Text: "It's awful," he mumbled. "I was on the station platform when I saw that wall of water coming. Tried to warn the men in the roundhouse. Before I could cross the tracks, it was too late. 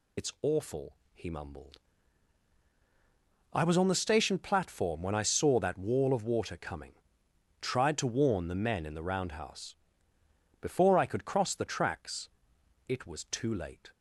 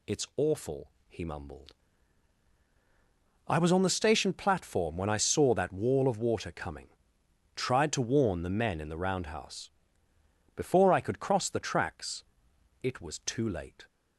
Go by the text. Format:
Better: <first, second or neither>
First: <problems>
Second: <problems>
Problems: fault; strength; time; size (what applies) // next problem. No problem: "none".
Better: second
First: loses the start of "It's"; at 0.1 s; 70 ms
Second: none